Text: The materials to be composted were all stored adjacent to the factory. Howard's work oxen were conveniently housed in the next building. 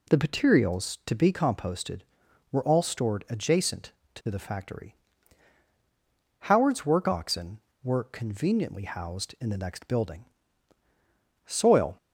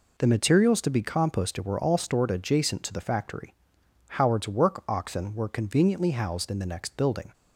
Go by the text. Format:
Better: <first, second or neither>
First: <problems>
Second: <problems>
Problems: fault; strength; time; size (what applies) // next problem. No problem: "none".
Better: second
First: goes on to say "Soil"; from 11.4 s on; 0.50 s long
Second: none